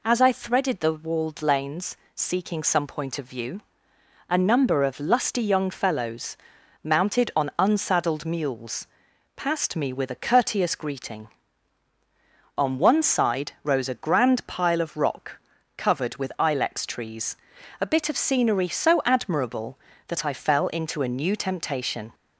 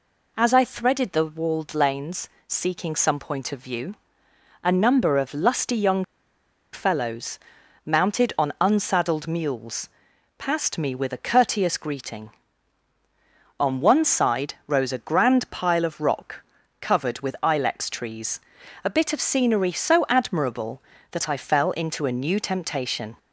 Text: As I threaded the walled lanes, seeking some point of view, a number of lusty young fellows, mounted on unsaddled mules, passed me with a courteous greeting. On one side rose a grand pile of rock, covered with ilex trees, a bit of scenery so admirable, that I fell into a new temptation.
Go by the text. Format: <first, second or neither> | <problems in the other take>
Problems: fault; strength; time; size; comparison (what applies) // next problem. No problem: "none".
first | pauses between "young" and "fellows"; noticeable; at 6.0 s; 0.68 s long